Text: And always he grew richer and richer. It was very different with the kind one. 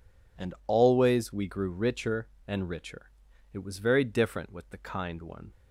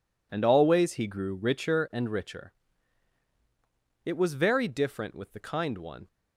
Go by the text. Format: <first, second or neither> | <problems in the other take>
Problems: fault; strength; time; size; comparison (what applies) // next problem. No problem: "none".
second | says "we" for "he"; at 1.3 s